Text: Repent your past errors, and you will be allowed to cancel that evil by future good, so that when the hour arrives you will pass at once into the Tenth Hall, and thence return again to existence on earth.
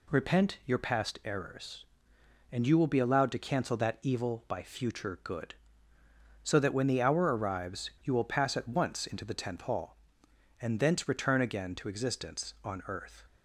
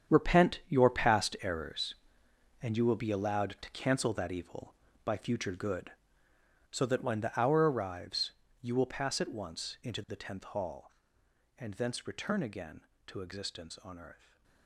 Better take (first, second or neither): first